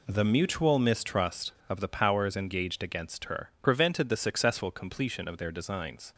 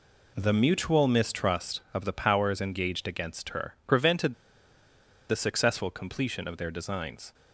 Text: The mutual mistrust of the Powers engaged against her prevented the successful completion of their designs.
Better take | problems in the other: first | pauses between "prevented" and "the"; noticeable; at 4.3 s; 0.96 s long

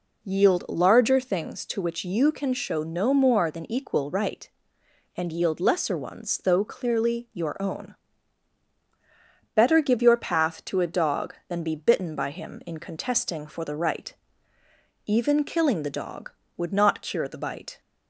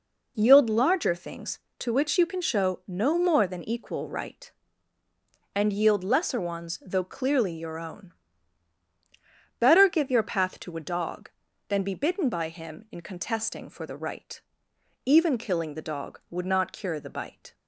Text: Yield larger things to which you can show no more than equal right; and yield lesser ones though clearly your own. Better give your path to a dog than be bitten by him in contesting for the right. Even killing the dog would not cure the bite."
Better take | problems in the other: neither | none

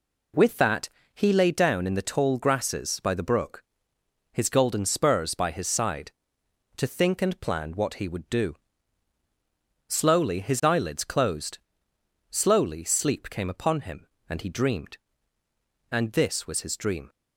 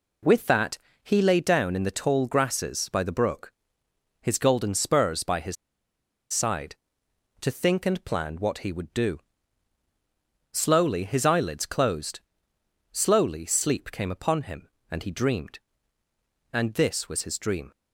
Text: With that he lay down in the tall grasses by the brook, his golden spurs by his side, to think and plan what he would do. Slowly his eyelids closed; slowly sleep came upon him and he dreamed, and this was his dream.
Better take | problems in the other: first | pauses between "that" and "he"; slight; at 0.7 s; 0.26 s long; slight in the first // pauses between "his" and "side"; noticeable; at 5.5 s; 0.77 s long

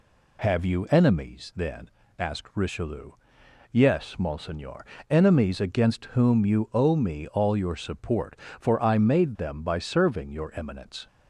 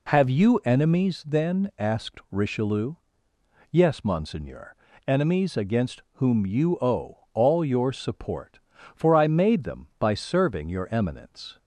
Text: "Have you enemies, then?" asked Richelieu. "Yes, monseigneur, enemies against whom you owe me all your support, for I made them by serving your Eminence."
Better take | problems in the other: first | skips "me"; at 7.2 s

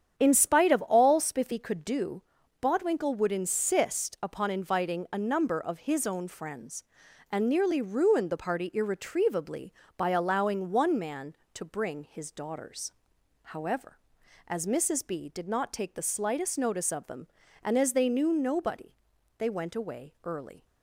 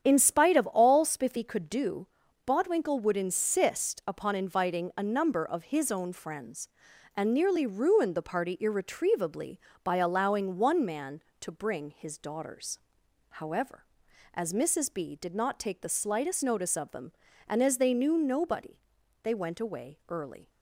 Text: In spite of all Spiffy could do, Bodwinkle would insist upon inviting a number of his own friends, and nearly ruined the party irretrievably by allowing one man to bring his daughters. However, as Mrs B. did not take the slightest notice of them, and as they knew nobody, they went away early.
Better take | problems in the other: neither | starts louder than the rest; strong; the same in both

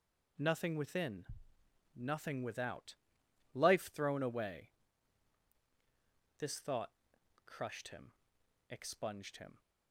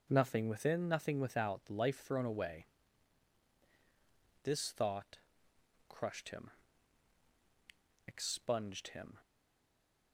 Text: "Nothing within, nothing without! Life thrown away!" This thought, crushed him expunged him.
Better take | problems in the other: first | pauses between "him" and "expunged"; strong; at 6.5 s; 1.5 s long; noticeable in the first // stays silent after the last word; slight; from 9.2 s on; 0.9 s long

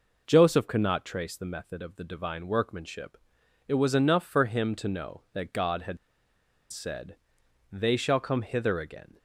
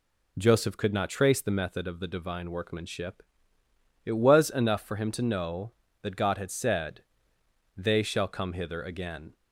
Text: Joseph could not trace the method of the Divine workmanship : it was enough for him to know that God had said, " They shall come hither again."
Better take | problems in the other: second | pauses between "had" and "said"; noticeable; at 5.9 s; 0.73 s long

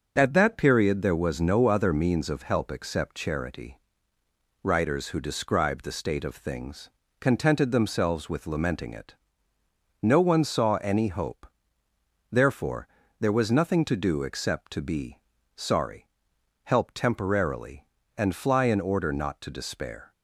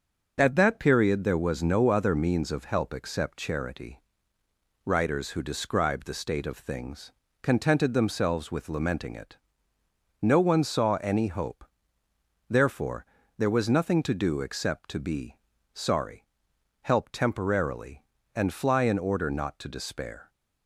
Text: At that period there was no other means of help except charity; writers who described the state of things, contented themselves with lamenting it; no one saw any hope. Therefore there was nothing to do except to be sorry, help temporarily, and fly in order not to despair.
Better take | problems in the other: neither | starts louder than the rest; noticeable; the same in both // pauses between "Therefore" and "there"; slight; the same in both // pauses between "be" and "sorry"; slight; the same in both

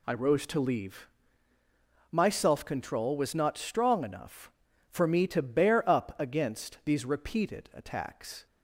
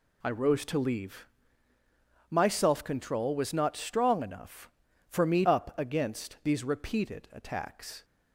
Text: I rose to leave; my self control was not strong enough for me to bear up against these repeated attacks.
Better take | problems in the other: first | skips "to bear"; at 5.4 s

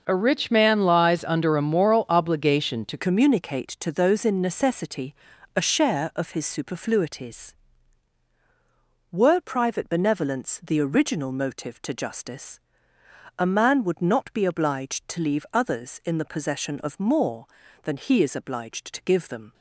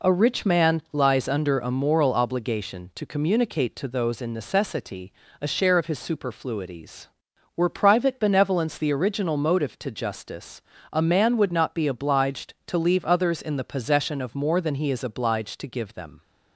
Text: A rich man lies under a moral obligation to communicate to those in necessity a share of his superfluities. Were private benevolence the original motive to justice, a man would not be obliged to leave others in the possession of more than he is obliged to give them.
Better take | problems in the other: second | changes voice at "communicate"; from 2.9 s on; 16.6 s long // pauses between "necessity" and "a"; at 5.1 s; 0.42 s long; slight in the second

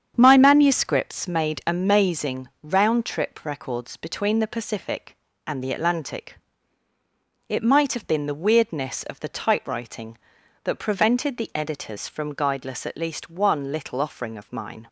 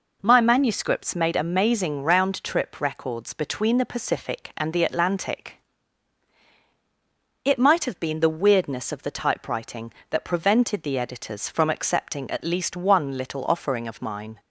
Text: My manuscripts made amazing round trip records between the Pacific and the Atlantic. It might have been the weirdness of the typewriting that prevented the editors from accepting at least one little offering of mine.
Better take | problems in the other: second | starts louder than the rest; strong; until 1.1 s; 8 dB // pauses between "amazing" and "round"; slight; at 2.4 s; 0.16 s long // says "guideless" for "accepting"; at 12.3 s

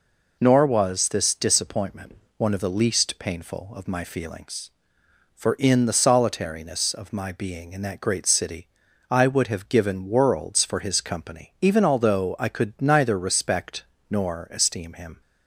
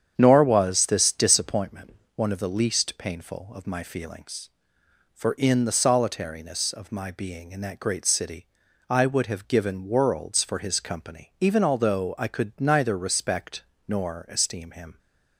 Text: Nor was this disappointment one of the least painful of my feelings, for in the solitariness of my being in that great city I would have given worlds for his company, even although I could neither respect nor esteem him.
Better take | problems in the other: first | starts louder than the rest; strong; until 1.7 s; 8.5 dB // pauses between "disappointment" and "one"; slight; at 1.9 s; 0.22 s long; slight in the first // pauses between "city" and "I"; at 8.4 s; 0.42 s long; also in the first // pauses between "respect" and "nor"; slight; at 13.6 s; 0.24 s long; slight in the first

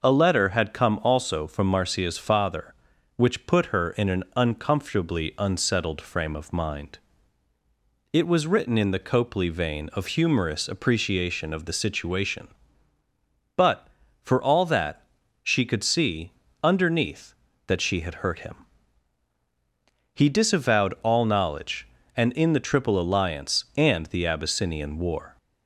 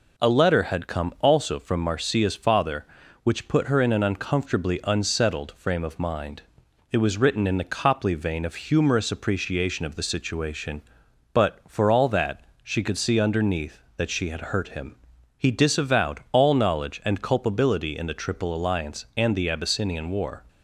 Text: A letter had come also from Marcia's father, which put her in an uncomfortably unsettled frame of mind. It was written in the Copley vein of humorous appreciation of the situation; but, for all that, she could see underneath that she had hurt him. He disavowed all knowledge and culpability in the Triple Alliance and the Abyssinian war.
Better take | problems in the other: second | pauses between "see" and "underneath"; slight; at 16.3 s; 0.32 s long // skips "culpability"; at 22.3 s

